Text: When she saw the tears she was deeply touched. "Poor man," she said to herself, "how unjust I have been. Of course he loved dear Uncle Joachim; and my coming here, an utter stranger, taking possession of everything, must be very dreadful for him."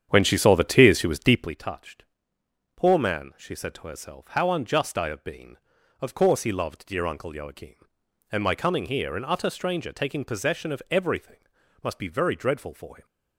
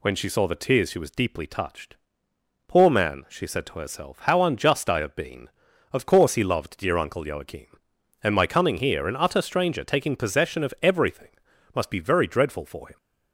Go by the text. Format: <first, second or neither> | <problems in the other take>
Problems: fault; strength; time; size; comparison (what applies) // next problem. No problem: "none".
second | starts louder than the rest; strong; until 1.6 s; 8.5 dB